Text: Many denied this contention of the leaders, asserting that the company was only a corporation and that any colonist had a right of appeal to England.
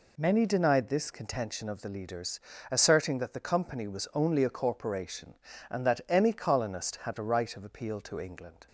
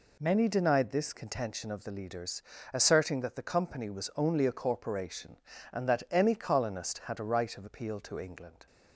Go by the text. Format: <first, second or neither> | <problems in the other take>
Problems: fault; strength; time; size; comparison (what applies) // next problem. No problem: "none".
neither | none